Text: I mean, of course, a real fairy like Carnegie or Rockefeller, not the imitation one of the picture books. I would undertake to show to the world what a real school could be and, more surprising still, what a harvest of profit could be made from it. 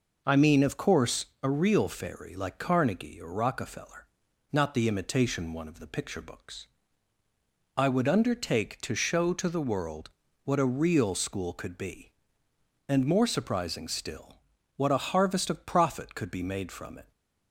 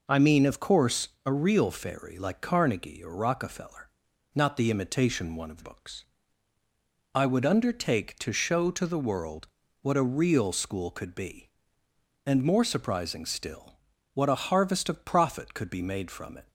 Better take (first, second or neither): first